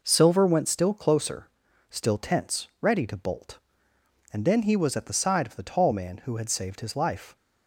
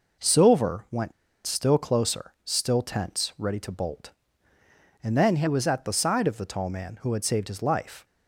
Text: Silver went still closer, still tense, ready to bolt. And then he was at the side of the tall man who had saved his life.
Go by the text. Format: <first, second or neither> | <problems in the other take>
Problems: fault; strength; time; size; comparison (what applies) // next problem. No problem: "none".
first | pauses between "went" and "still"; slight; at 1.1 s; 0.34 s long